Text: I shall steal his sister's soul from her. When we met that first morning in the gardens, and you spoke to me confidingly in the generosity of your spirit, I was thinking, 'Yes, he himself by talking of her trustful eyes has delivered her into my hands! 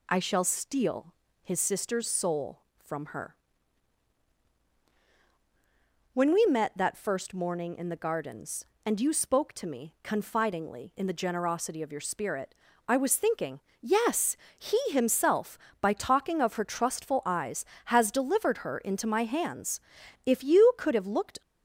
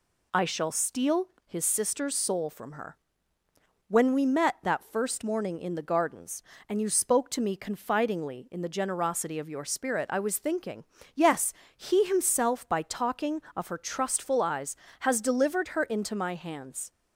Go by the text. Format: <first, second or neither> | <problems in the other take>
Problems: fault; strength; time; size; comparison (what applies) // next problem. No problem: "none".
second | pauses between "steal" and "his"; slight; at 1.1 s; 0.30 s long; slight in the second // goes on to say "If you could have looked"; noticeable; from 20.2 s on; 1.1 s long